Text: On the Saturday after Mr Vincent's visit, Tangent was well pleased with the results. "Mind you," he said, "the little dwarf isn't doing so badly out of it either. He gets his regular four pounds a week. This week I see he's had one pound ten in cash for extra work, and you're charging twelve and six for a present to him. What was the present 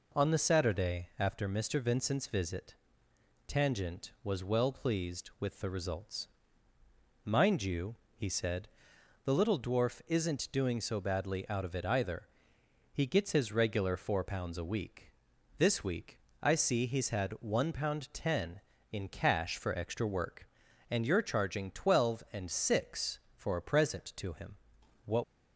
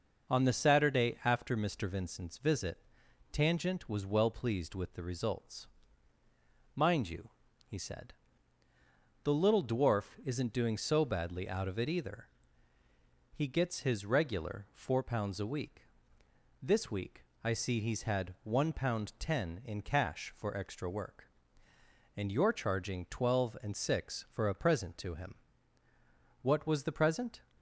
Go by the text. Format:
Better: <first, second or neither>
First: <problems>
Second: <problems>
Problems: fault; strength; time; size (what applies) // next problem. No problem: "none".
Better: second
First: pauses between "week" and "I"; slight; at 16.1 s; 0.24 s long // stops before "was the present"; at 25.2 s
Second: pauses between "week" and "I"; slight; at 17.2 s; 0.16 s long